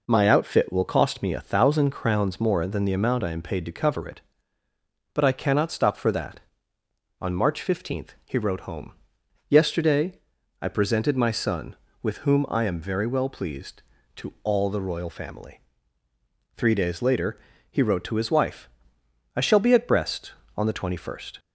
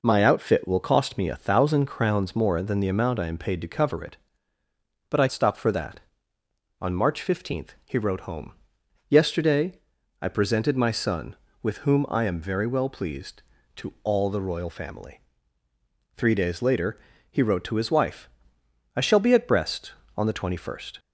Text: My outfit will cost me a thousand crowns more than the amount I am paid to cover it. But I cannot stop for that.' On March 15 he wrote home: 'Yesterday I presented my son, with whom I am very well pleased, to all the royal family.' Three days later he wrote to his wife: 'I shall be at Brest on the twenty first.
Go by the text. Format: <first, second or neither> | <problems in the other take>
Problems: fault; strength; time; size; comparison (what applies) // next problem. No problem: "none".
first | skips "cannot"; at 5.2 s // pauses between "Yesterday" and "I"; at 9.7 s; 0.42 s long; also in the first // pauses between "later" and "he"; slight; at 16.9 s; 0.32 s long; slight in the first